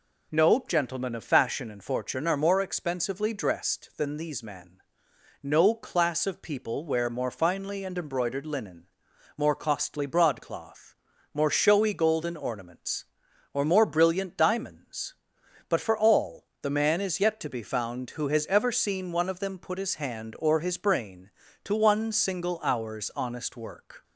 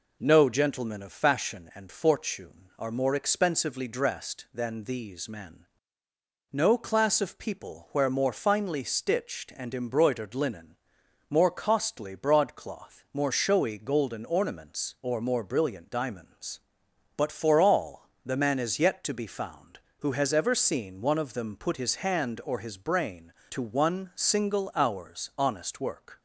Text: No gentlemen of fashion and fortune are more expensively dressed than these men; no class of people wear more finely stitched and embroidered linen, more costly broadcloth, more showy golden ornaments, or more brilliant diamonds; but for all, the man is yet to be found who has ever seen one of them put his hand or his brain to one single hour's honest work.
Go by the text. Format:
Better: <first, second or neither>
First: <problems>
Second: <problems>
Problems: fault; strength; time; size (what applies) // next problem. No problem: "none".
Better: second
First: skips "stitched"; at 7.8 s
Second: none